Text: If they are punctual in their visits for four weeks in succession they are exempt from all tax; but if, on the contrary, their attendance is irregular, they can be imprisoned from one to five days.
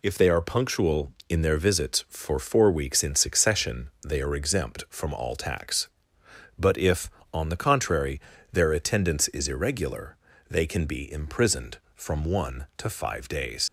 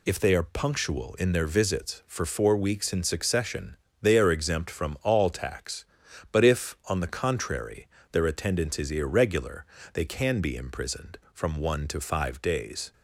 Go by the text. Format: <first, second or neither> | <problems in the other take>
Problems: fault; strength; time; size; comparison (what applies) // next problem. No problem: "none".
second | pauses between "succession" and "they"; slight; at 3.8 s; 0.18 s long; slight in the second // leaves "days" unfinished; at 13.6 s; 80 ms